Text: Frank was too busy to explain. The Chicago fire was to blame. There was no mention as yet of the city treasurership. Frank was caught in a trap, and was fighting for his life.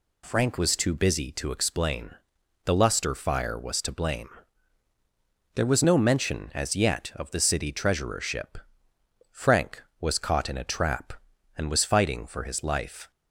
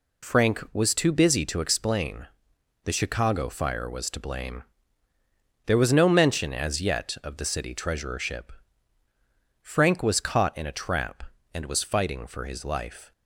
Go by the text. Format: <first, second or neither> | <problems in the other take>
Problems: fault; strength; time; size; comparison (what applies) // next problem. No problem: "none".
second | says "Luster" for "Chicago"; at 2.7 s